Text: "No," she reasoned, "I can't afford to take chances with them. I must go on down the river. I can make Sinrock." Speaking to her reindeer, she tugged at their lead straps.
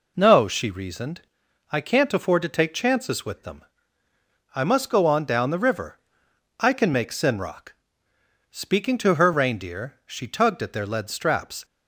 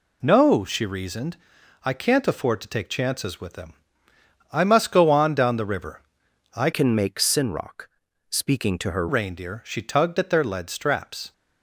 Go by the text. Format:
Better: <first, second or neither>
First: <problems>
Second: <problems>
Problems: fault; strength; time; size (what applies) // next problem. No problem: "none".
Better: first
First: none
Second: changes voice from "can" to "her"; from 6.7 to 9.0 s; 2.3 s long